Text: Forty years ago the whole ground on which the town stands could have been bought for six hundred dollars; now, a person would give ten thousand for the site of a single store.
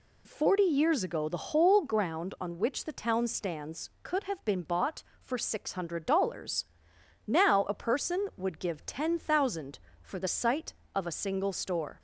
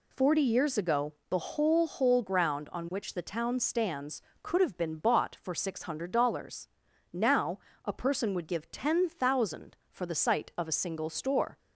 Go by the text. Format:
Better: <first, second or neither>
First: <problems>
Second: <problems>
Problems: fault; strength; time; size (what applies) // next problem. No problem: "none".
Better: first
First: none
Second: pauses between "ago" and "the"; slight; at 1.1 s; 0.16 s long // says "whole" twice; at 1.8 s